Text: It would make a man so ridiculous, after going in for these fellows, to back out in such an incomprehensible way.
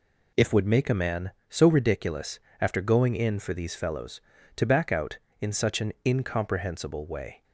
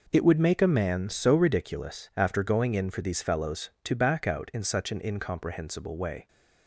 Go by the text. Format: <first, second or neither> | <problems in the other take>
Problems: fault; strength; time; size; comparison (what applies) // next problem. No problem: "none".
second | says "If" for "It"; at 0.3 s